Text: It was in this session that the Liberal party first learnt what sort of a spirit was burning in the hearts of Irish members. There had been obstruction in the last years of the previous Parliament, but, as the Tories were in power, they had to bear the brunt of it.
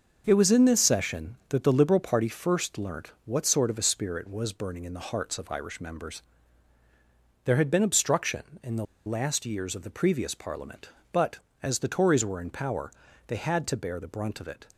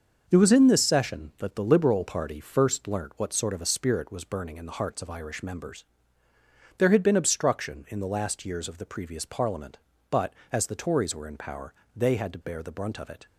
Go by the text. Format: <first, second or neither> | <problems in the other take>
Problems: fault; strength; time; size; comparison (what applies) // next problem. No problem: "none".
second | starts louder than the rest; noticeable; until 1.2 s; 6 dB; also in the second // pauses between "the" and "last"; slight; at 8.8 s; 0.22 s long